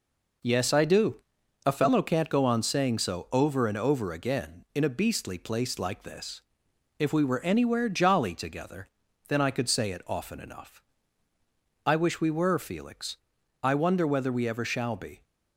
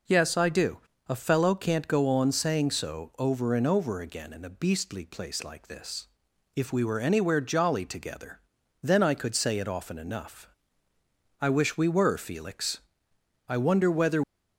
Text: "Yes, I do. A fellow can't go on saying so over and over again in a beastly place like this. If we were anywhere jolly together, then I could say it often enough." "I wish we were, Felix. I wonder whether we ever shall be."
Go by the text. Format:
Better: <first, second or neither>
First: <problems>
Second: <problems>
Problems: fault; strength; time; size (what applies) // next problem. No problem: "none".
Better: first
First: none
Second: stops before "we ever shall be"; at 14.2 s